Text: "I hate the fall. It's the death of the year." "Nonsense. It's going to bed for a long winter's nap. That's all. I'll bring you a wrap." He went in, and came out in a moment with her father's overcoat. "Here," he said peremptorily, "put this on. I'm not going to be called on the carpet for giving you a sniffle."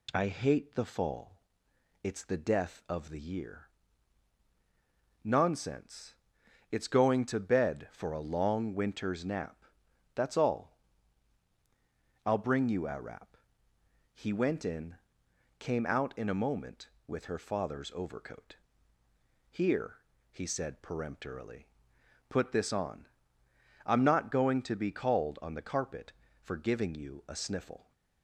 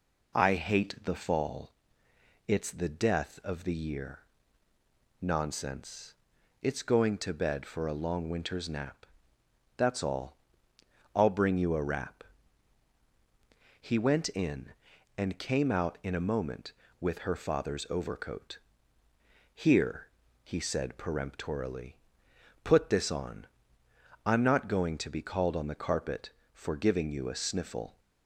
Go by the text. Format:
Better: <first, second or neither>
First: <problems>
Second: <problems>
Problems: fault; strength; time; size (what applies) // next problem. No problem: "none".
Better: second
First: skips "and"; at 15.2 s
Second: none